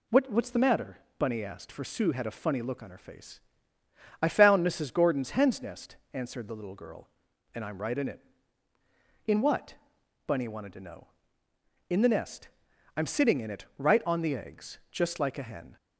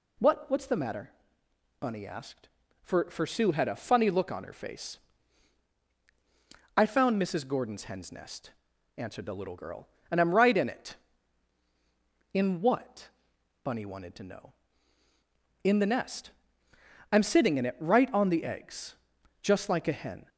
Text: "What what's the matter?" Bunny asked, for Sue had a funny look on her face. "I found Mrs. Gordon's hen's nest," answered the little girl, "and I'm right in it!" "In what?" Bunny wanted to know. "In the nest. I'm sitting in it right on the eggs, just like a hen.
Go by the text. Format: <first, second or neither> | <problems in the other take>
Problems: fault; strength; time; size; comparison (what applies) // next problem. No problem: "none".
first | says "for" twice; at 3.1 s